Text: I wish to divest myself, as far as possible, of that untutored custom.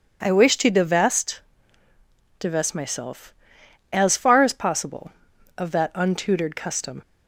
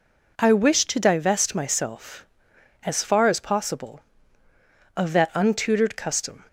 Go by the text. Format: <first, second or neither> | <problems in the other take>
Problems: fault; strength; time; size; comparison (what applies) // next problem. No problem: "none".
second | says "divest" twice; at 2.3 s